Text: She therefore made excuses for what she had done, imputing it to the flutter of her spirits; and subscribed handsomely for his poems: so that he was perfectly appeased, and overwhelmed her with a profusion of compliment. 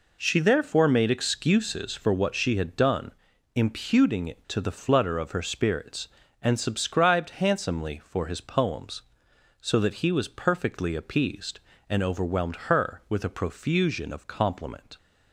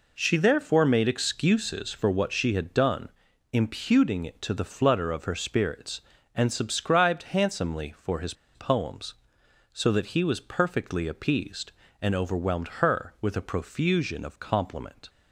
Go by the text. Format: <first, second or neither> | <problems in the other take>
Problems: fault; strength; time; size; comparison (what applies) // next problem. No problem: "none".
first | pauses between "his" and "poems"; slight; at 8.3 s; 0.21 s long // pauses between "overwhelmed" and "her"; slight; at 12.6 s; 0.16 s long; slight in the first